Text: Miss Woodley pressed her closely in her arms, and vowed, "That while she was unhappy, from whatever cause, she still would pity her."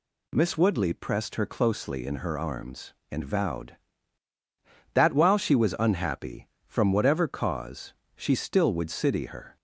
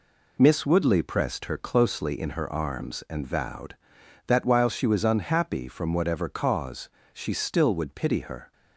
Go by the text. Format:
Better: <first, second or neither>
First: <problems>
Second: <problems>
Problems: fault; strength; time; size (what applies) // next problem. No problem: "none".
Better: second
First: says "city" for "pity"; at 8.9 s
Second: none